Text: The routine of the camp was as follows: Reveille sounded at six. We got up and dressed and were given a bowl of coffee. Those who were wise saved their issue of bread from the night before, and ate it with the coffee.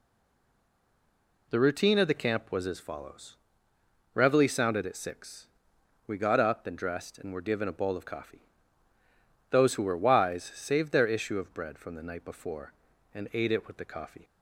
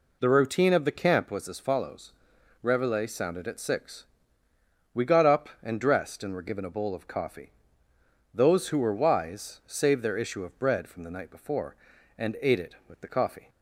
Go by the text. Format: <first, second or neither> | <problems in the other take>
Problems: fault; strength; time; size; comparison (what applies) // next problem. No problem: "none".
second | stays silent before the first word; noticeable; until 1.4 s; 1.4 s long